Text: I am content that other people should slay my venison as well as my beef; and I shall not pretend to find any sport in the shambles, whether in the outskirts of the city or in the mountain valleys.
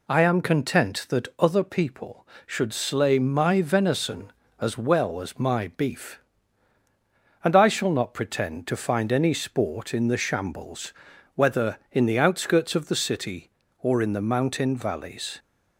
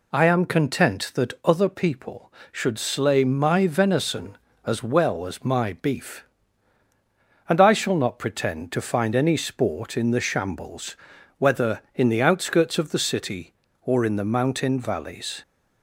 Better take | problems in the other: neither | none

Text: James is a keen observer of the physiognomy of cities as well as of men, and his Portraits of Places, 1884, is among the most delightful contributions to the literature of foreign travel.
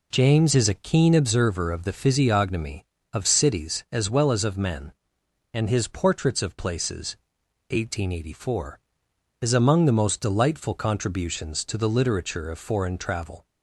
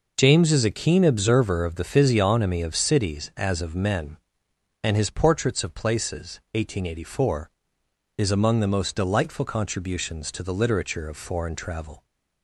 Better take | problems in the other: first | skips "as well"; at 3.3 s

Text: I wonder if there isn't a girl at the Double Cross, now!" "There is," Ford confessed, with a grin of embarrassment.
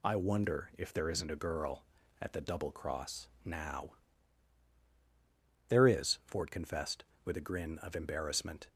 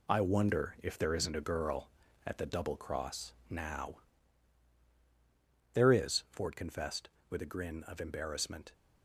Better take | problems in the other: first | gets quieter; strong; throughout; 7.5 dB

